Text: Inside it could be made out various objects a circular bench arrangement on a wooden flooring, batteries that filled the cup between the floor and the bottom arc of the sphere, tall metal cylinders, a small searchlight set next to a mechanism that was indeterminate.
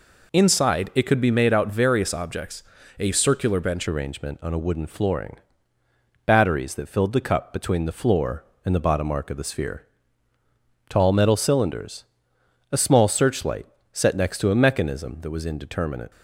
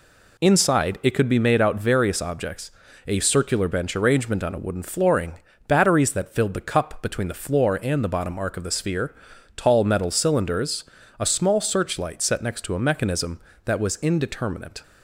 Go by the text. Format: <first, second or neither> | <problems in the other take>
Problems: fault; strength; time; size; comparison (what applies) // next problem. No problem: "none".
second | pauses between "objects" and "a"; at 2.6 s; 0.38 s long; also in the second // changes voice at "arrangement"; from 3.8 s on; 12.3 s long // pauses between "searchlight" and "set"; slight; at 13.6 s; 0.26 s long